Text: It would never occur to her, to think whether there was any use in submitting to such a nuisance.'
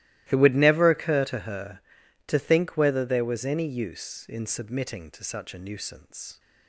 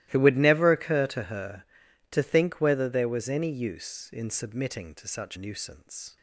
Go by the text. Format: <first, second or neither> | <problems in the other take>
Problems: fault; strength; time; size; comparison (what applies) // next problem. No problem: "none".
first | starts louder than the rest; strong; until 1.1 s; 16 dB; strong in the first // skips "a"; at 5.3 s